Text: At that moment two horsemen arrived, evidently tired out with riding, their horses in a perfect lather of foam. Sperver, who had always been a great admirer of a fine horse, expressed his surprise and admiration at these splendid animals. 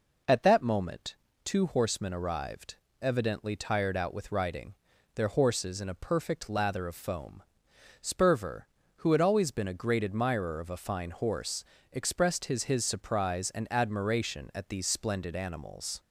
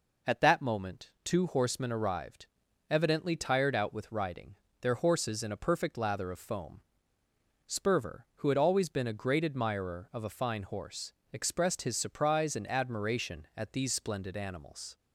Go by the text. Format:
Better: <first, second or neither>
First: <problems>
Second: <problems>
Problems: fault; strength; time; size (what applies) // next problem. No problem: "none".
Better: second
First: pauses between "moment" and "two"; slight; at 1.1 s; 0.28 s long // says "his" twice; at 12.6 s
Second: none